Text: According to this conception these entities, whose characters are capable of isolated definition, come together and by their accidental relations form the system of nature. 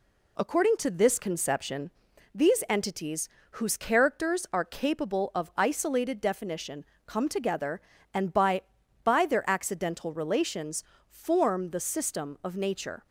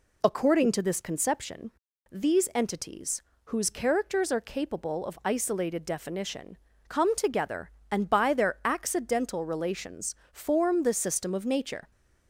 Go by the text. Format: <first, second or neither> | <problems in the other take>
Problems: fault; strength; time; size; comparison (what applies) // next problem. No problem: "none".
second | pauses between "conception" and "these"; at 1.9 s; 0.44 s long; also in the second // says "by" twice; at 9.0 s // pauses between "relations" and "form"; slight; at 10.8 s; 0.24 s long; slight in the second